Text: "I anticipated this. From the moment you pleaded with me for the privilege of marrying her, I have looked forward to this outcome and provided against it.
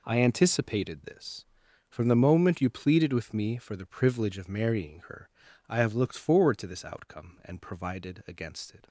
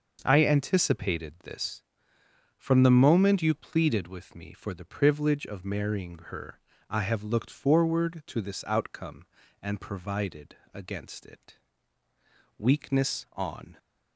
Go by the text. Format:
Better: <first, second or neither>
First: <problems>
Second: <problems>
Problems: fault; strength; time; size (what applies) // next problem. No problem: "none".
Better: first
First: none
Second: pauses between "provided" and "against"; slight; at 10.5 s; 0.16 s long // goes on to say "Weakness on"; noticeable; from 12.5 s on; 1.1 s long